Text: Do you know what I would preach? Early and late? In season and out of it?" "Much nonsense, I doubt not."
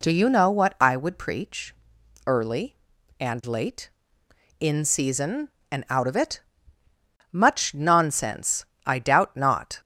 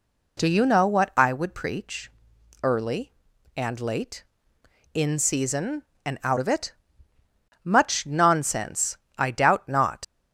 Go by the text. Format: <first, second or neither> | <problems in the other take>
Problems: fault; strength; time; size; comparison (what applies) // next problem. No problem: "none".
first | leaves "not" unfinished; at 10.0 s; 75 ms